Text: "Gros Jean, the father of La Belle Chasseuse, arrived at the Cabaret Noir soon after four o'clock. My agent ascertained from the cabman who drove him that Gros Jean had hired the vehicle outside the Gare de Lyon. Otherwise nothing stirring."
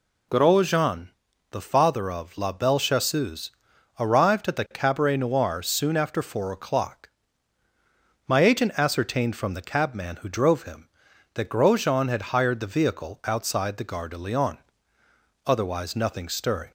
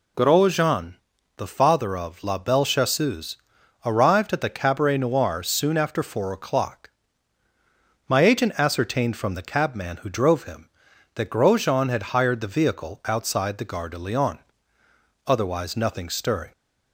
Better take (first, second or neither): neither